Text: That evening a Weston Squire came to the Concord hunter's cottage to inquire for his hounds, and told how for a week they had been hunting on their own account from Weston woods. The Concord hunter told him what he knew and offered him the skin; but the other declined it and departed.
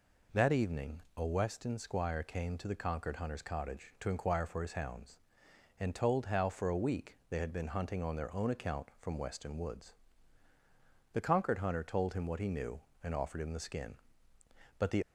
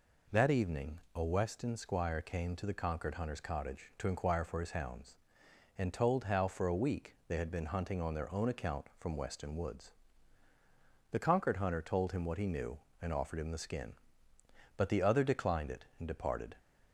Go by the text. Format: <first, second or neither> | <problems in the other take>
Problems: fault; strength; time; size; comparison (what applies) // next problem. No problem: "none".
second | pauses between "evening" and "a"; slight; at 1.0 s; 0.16 s long; slight in the second // stops before "other declined it and departed"; at 15.0 s